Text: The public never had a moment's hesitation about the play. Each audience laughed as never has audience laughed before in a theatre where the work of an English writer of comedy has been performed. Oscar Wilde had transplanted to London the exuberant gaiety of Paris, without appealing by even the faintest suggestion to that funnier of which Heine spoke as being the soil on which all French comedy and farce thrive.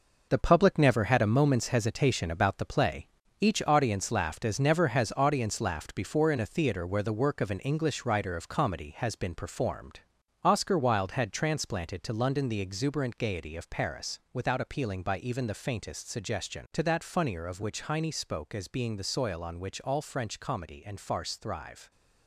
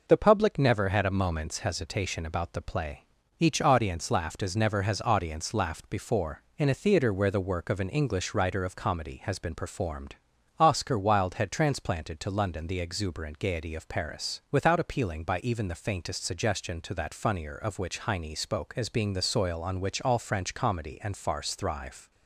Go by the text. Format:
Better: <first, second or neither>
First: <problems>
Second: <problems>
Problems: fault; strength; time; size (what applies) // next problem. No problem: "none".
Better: second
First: gets quieter; strong; throughout; 8 dB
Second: none